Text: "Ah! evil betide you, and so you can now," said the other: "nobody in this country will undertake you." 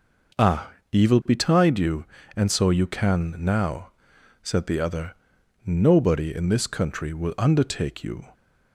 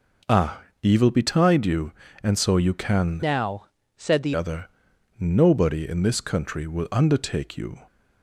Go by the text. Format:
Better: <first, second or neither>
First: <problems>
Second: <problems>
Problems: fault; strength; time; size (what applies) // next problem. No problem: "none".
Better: first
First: none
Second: changes voice from "now" to "the"; from 3.2 to 4.3 s; 1.1 s long